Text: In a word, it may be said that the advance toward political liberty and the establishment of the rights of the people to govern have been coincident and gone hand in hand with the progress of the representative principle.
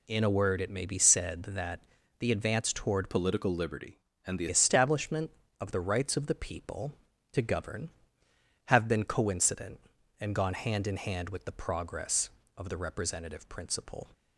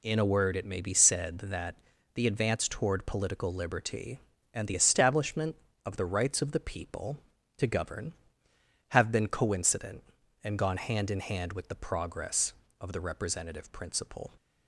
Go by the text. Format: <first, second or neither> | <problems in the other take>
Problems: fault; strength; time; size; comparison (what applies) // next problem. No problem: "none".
second | pauses between "that" and "the"; at 1.8 s; 0.38 s long; also in the second // changes voice from "political" to "the"; from 3.0 to 4.4 s; 1.4 s long